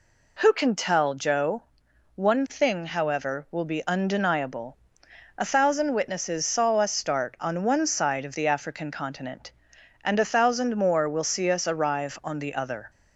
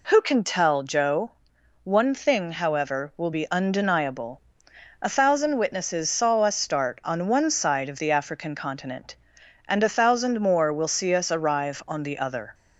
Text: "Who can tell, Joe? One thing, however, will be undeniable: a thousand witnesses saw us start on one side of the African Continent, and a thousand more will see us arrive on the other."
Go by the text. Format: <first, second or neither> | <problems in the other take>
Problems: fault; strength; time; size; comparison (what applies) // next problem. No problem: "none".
neither | none